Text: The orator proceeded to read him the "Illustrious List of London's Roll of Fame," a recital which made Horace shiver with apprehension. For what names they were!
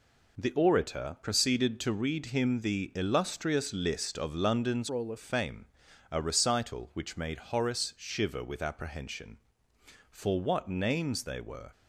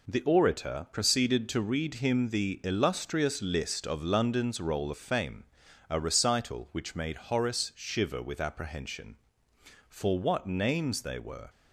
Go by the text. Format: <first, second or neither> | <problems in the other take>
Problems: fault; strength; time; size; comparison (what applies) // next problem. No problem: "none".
second | changes voice from "Roll" to "of"; from 4.8 to 5.1 s; 0.3 s long